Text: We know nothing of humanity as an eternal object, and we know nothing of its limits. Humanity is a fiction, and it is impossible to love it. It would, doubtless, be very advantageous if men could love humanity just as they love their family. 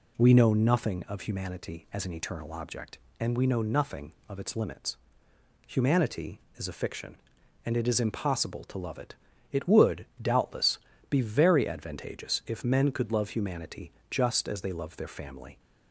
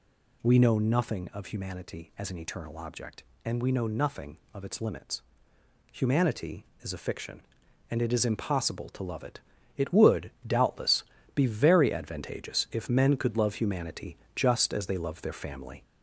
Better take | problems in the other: first | gets louder; slight; throughout; 3.5 dB // pauses between "humanity" and "just"; slight; at 14.1 s; 0.18 s long; slight in the first

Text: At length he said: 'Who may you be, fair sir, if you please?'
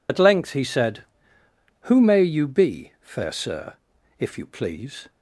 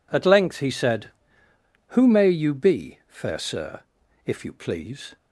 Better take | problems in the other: second | loses the start of "At"; at 0.0 s; 60 ms

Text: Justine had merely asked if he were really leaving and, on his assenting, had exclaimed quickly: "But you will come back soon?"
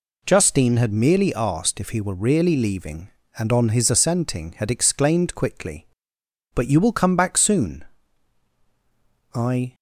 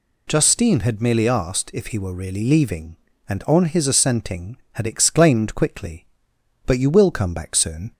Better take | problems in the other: second | goes on to say "I"; slight; from 9.3 s on; 0.40 s long

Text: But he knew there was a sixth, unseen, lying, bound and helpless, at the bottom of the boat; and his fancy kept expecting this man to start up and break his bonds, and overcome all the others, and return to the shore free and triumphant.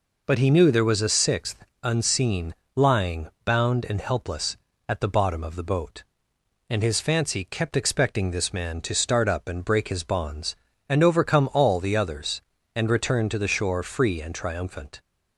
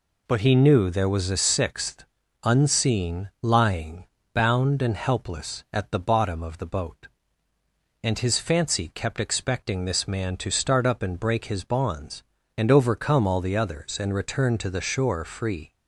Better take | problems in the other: first | stops before "and triumphant"; at 15.7 s

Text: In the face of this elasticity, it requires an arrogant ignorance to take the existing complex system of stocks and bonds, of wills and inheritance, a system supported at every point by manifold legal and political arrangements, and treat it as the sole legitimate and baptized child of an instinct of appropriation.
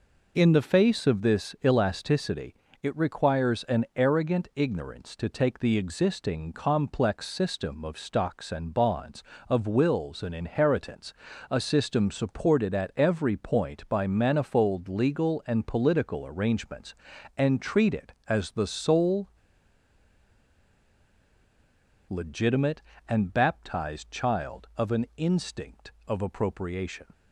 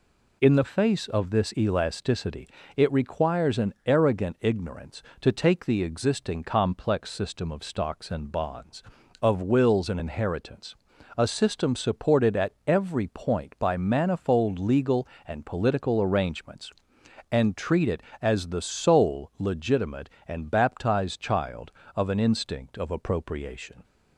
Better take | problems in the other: second | pauses between "sole" and "legitimate"; strong; at 19.3 s; 2.7 s long

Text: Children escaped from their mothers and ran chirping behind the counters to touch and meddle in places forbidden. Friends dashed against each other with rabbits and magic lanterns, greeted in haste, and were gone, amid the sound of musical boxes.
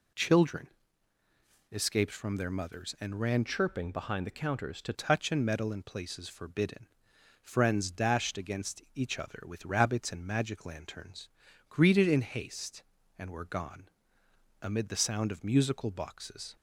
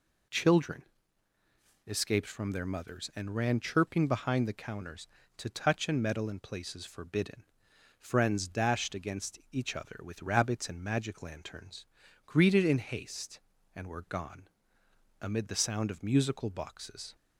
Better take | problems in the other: second | pauses between "Children" and "escaped"; at 0.6 s; 1.0 s long; also in the second // changes voice from "chirping" to "to"; from 3.4 to 4.9 s; 1.5 s long

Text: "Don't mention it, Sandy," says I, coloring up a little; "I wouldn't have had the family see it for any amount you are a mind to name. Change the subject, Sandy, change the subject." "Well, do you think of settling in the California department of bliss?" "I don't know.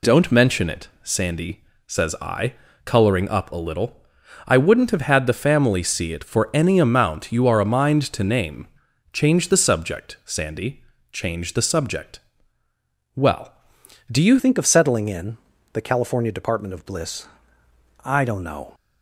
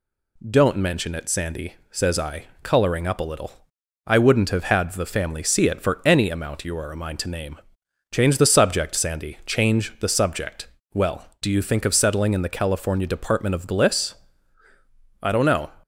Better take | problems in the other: second | changes voice at "think"; from 14.3 s on; 4.4 s long // pauses between "in" and "the"; slight; at 15.3 s; 0.34 s long

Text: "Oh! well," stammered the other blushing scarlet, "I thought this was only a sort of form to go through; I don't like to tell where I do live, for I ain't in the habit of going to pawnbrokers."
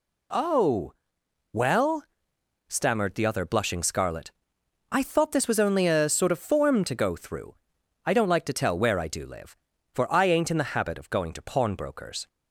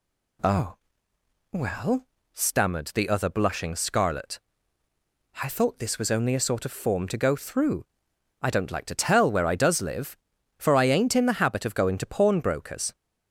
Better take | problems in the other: first | says "does" for "do"; at 9.5 s

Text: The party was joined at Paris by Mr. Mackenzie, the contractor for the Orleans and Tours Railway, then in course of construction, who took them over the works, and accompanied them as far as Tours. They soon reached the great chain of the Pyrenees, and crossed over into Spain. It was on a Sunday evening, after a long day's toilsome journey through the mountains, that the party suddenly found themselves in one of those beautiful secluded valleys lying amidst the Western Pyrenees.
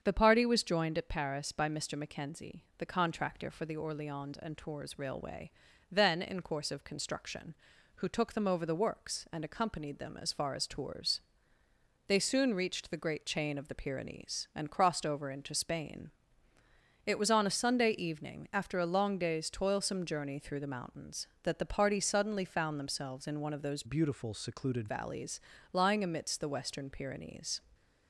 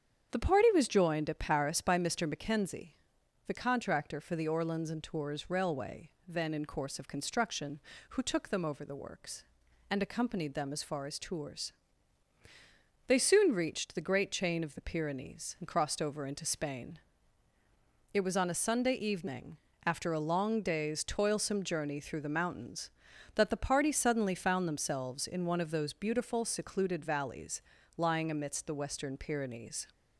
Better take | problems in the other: second | starts louder than the rest; strong; until 1.0 s; 7.5 dB; strong in the second // changes voice from "beautiful" to "secluded"; from 23.8 to 24.8 s; 1.0 s long // pauses between "valleys" and "lying"; slight; at 25.3 s; 0.34 s long; slight in the second

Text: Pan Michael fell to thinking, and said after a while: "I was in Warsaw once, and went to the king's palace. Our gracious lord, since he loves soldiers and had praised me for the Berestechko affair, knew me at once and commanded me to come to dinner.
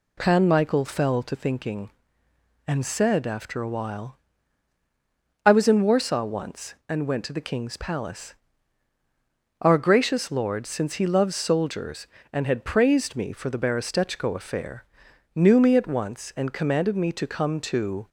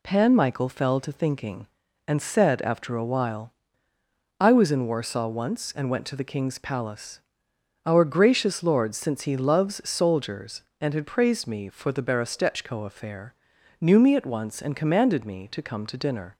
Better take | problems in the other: second | stops before "dinner"; at 18.0 s

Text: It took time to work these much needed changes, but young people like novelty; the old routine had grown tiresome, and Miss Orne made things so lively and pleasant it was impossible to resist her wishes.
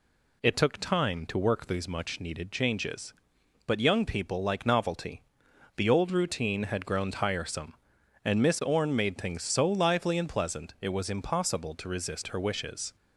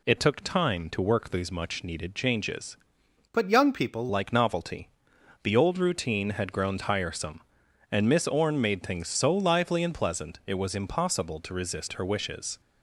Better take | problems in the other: first | changes voice from "but" to "people"; from 3.3 to 4.0 s; 0.7 s long

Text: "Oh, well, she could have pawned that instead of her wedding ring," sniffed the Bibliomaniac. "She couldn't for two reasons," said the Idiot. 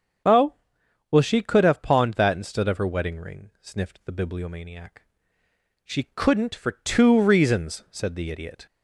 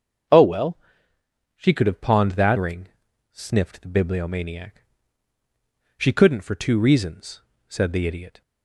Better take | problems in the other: first | starts louder than the rest; until 2.0 s; 6.5 dB; strong in the first // skips "instead of her wedding"; at 2.5 s

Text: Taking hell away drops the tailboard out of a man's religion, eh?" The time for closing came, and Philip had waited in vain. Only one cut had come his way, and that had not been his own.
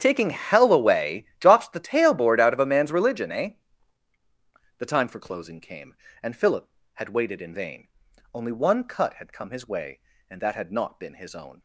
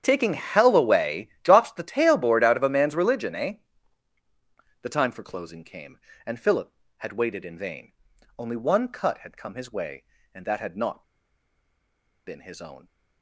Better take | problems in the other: first | starts louder than the rest; strong; until 1.0 s; 9 dB; strong in the first // pauses between "not" and "been"; at 11.0 s; 1.2 s long

